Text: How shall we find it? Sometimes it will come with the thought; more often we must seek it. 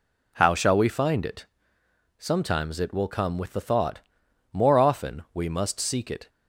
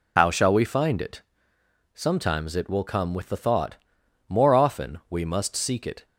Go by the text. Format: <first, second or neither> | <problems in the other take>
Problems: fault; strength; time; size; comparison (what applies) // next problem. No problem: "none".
first | loses the start of "How"; at 0.1 s; 50 ms